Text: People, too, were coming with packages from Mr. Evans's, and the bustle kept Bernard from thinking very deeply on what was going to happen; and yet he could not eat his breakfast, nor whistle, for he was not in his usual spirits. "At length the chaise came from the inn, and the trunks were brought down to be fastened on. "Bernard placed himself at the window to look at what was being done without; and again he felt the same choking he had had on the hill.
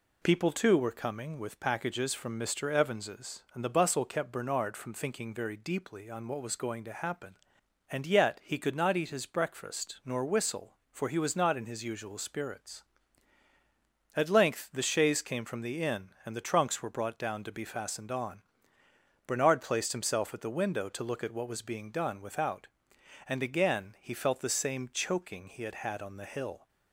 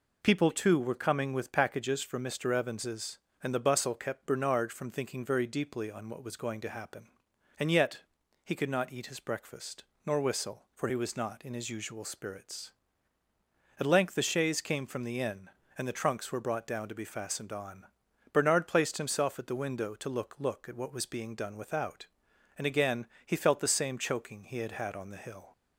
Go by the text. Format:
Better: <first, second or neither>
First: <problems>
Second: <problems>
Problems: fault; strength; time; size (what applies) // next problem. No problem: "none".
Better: first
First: none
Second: pauses between "yet" and "he"; at 8.0 s; 0.42 s long // says "look" twice; at 20.3 s // pauses between "again" and "he"; slight; at 23.0 s; 0.18 s long